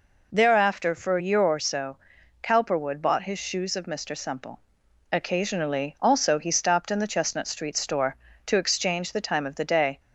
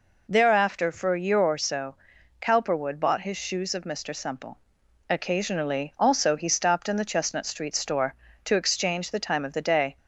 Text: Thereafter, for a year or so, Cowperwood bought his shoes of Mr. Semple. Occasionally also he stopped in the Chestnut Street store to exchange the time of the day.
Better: neither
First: none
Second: none

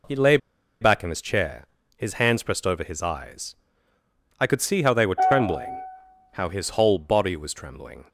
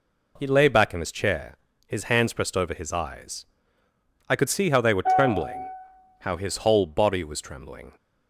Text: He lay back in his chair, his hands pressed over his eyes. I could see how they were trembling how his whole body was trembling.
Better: second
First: pauses between "lay" and "back"; at 0.3 s; 0.44 s long // pauses between "trembling" and "how"; noticeable; at 5.7 s; 0.62 s long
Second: pauses between "trembling" and "how"; noticeable; at 5.5 s; 0.62 s long

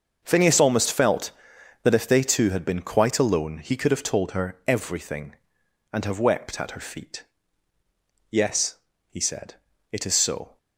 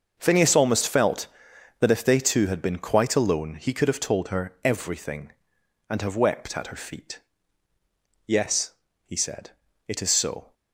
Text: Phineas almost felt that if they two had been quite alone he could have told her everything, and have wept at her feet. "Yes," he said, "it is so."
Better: neither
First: starts louder than the rest; until 1.2 s; 6.5 dB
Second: starts louder than the rest; until 1.1 s; 6.5 dB

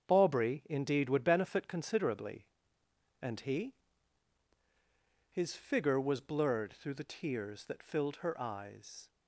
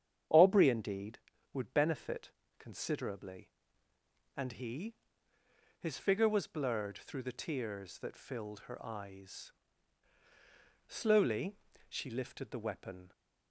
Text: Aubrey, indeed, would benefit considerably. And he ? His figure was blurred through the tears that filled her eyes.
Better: first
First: starts louder than the rest; strong; until 1.1 s; 7.5 dB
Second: starts louder than the rest; strong; until 1.6 s; 8.5 dB // pauses between "benefit" and "considerably"; slight; at 2.2 s; 0.28 s long // goes on to say "Slowly she lifted the weapon"; strong; from 10.8 s on; 2.2 s long

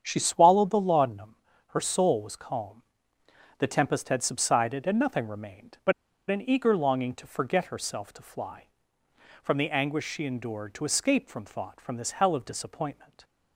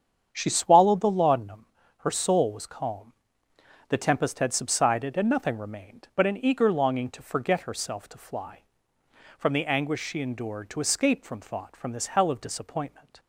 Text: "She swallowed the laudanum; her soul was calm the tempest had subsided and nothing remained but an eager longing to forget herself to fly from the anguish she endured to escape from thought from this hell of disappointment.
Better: second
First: starts louder than the rest; strong; until 1.0 s; 8 dB // pauses between "calm" and "the"; noticeable; at 2.8 s; 0.76 s long // pauses between "but" and "an"; at 5.9 s; 0.37 s long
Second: starts louder than the rest; strong; until 1.3 s; 8 dB // pauses between "calm" and "the"; noticeable; at 3.1 s; 0.76 s long

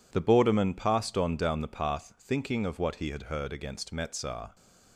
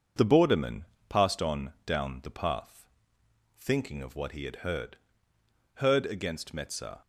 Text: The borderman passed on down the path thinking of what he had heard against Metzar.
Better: first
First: none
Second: pauses between "borderman" and "passed"; slight; at 0.8 s; 0.24 s long // pauses between "path" and "thinking"; noticeable; at 2.8 s; 0.72 s long // says "heard" twice; at 5.7 s

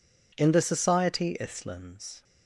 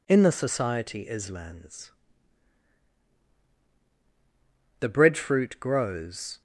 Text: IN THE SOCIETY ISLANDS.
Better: first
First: none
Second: goes on to say "The breadfruit grows"; from 4.8 s on; 1.6 s long

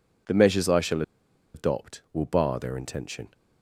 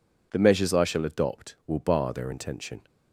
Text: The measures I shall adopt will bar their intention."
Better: second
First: pauses between "shall" and "adopt"; noticeable; at 1.0 s; 0.52 s long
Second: none

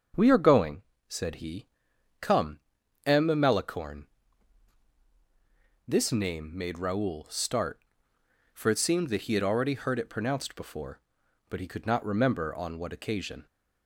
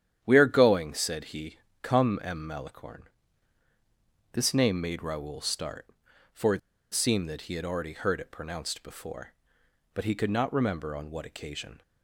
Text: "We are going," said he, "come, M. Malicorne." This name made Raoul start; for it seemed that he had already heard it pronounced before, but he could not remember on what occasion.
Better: first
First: starts louder than the rest; until 1.4 s; 6.5 dB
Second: starts louder than the rest; strong; until 1.2 s; 10 dB // pauses between "it" and "seemed"; slight; at 6.5 s; 0.33 s long

